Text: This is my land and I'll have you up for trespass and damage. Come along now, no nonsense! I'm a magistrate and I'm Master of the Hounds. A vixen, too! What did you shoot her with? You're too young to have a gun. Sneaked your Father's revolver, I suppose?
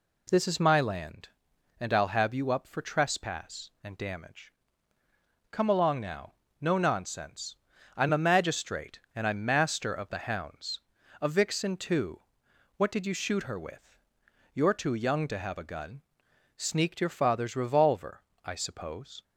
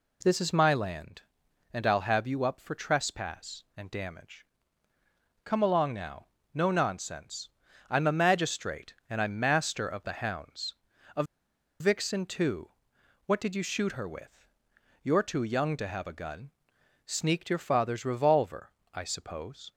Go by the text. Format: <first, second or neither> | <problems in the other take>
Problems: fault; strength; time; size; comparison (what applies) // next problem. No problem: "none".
first | pauses between "A" and "vixen"; noticeable; at 11.2 s; 0.56 s long